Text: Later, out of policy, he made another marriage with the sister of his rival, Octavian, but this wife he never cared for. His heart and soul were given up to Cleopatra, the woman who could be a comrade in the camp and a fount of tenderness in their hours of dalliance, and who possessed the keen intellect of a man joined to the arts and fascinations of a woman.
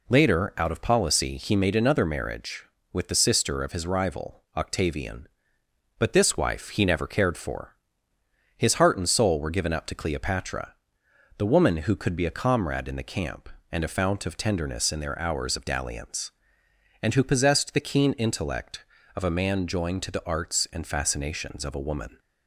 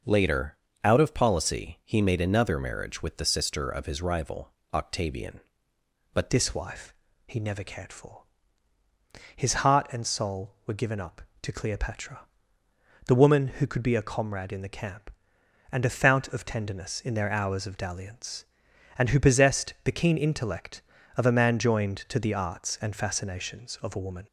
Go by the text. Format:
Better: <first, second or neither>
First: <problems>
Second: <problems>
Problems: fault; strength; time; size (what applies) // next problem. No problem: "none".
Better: first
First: none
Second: changes voice at "this"; from 6.2 s on; 18.0 s long // pauses between "wife" and "he"; slight; at 6.9 s; 0.36 s long